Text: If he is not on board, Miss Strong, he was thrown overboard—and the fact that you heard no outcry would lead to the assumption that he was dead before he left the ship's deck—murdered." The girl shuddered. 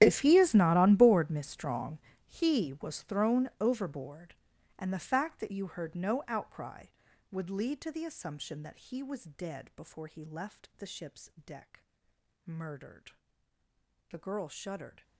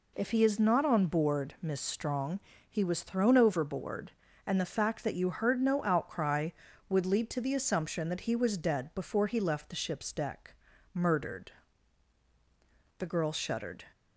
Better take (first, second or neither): second